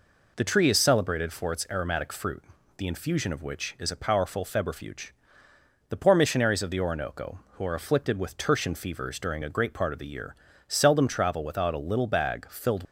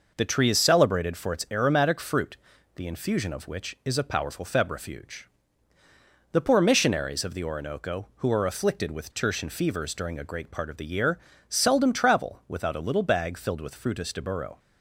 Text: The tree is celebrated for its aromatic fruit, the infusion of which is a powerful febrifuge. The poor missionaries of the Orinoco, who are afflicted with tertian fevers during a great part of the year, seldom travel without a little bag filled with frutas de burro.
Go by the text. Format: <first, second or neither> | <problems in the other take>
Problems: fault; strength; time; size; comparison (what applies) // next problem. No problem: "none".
second | stops before "with frutas de burro"; at 12.8 s